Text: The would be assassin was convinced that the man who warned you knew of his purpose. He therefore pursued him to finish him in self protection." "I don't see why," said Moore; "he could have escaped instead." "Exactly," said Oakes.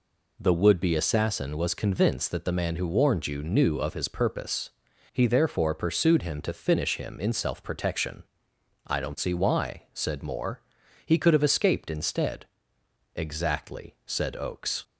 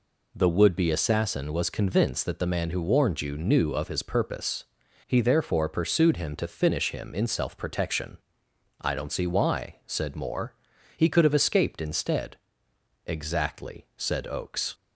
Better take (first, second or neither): neither